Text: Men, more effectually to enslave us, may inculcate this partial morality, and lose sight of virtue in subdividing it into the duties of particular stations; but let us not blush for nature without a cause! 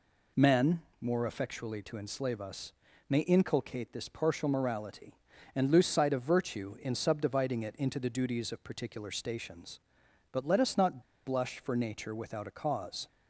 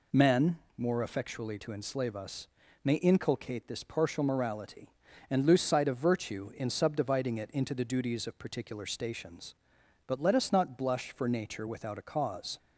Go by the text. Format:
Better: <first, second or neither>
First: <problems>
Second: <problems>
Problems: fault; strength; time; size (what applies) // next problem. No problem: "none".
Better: second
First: pauses between "not" and "blush"; slight; at 11.0 s; 0.24 s long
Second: none